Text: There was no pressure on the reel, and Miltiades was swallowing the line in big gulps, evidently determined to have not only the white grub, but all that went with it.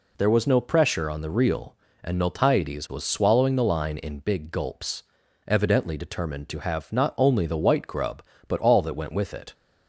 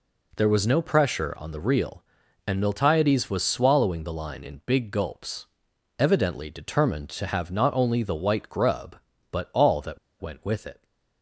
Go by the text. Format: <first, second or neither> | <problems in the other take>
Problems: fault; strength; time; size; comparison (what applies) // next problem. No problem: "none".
first | pauses between "that" and "went"; slight; at 9.9 s; 0.22 s long